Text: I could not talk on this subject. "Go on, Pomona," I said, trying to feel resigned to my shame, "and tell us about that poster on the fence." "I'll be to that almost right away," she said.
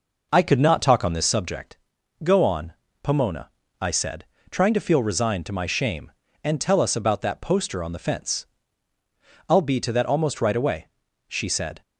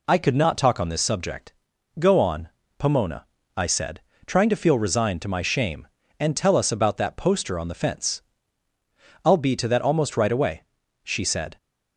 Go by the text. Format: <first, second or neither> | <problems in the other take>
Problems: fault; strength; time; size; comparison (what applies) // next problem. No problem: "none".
second | starts louder than the rest; noticeable; until 1.6 s; 5 dB